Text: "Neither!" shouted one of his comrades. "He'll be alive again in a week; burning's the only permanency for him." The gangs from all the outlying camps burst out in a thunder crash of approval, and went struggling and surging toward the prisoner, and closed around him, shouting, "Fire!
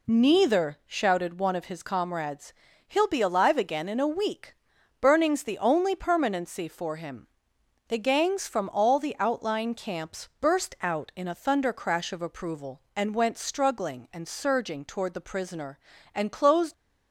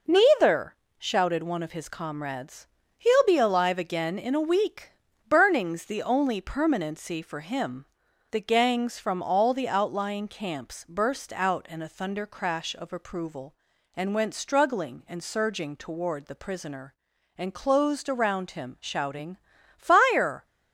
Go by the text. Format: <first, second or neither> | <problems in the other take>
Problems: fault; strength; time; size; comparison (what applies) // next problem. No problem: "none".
second | stops before "around him shouting Fire"; at 16.7 s